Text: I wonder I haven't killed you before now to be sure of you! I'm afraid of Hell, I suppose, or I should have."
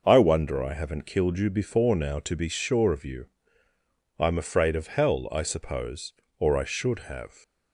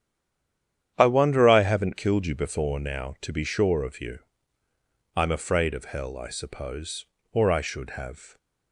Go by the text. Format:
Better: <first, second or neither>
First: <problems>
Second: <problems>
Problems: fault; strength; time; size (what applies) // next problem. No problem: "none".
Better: first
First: none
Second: stays silent before the first word; slight; until 0.9 s; 0.9 s long // starts louder than the rest; strong; until 1.9 s; 9.5 dB